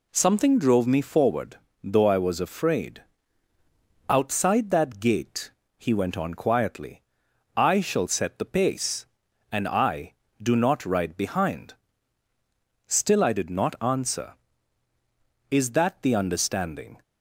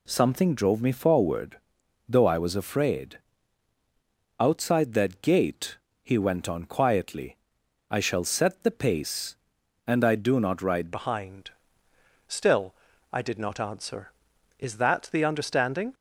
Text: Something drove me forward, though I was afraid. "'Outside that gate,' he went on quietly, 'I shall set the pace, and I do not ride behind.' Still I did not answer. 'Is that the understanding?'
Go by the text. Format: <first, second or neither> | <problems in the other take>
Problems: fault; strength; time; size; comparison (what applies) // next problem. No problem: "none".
first | changes voice at "behind"; from 10.9 s on; 5.0 s long // pauses between "Still" and "I"; at 12.7 s; 0.40 s long